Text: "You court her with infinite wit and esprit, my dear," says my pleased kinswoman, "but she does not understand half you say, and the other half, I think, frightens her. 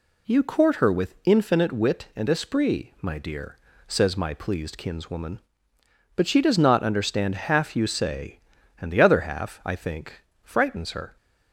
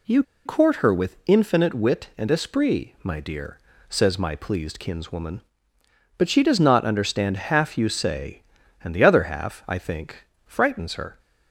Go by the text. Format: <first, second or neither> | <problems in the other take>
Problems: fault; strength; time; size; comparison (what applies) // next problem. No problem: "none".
first | pauses between "You" and "court"; slight; at 0.2 s; 0.22 s long